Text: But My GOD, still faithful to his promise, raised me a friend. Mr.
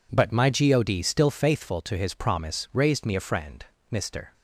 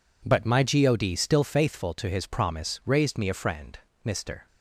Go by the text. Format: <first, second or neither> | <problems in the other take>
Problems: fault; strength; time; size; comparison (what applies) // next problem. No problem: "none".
neither | none